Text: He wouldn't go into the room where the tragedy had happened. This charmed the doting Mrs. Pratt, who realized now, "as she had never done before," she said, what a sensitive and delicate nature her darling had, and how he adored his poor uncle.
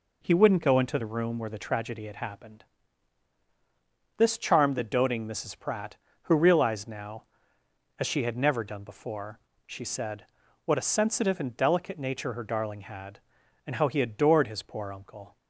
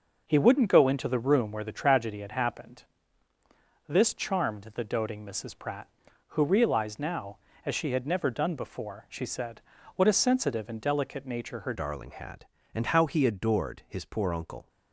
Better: first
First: none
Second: changes voice at "darling"; from 11.7 s on; 2.9 s long

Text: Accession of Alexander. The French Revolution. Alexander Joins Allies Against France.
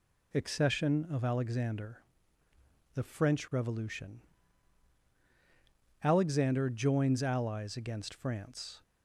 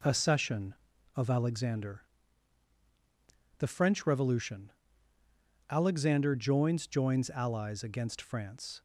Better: first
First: none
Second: says "Joins" twice; at 6.8 s

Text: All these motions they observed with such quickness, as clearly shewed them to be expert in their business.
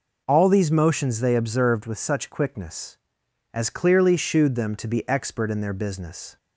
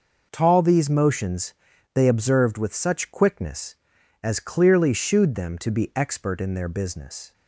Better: first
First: none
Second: says "Tall" for "All"; at 0.3 s // pauses between "motions" and "they"; at 1.5 s; 0.40 s long

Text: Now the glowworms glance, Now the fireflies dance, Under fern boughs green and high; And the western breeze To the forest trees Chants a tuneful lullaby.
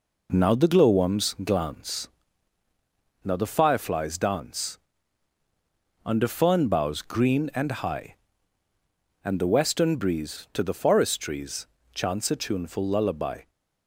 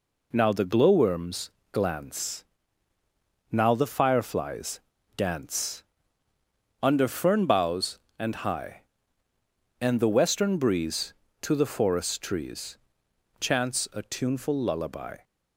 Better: first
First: pauses between "trees" and "Chants"; slight; at 11.6 s; 0.30 s long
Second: pauses between "glowworms" and "glance"; slight; at 1.4 s; 0.24 s long // pauses between "fireflies" and "dance"; slight; at 4.7 s; 0.35 s long // skips "green"; at 8.0 s // pauses between "trees" and "Chants"; noticeable; at 12.7 s; 0.62 s long

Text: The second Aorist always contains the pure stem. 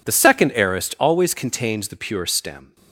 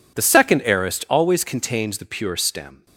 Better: neither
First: none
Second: none

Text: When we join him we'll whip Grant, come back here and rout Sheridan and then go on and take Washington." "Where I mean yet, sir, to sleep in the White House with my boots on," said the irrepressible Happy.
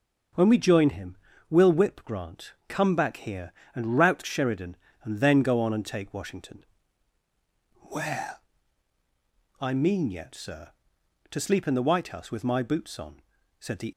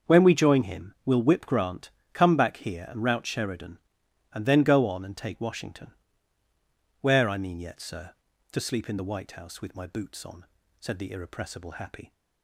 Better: second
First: starts louder than the rest; until 1.6 s; 6 dB // pauses between "him" and "we'll"; slight; at 1.1 s; 0.34 s long // pauses between "Where" and "I"; at 8.3 s; 1.2 s long // stops before "irrepressible Happy"; at 13.9 s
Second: starts louder than the rest; until 1.1 s; 6.5 dB

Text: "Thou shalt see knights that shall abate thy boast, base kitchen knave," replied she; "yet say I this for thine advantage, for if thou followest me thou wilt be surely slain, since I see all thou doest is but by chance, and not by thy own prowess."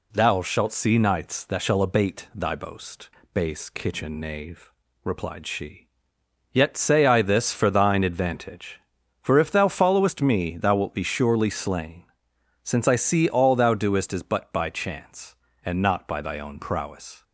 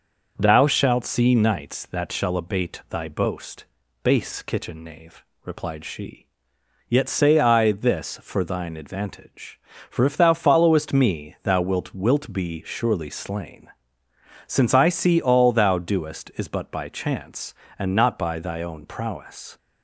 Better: first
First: none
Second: says "wilt" twice; at 11.9 s

